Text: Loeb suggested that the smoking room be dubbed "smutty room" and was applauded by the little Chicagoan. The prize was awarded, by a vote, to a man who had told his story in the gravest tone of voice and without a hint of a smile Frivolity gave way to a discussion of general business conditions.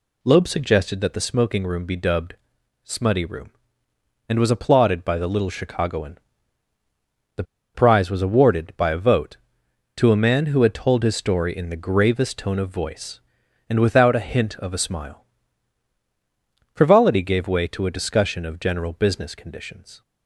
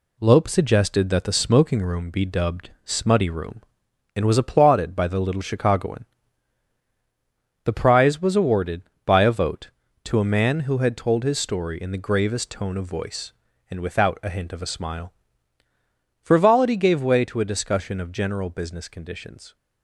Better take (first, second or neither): second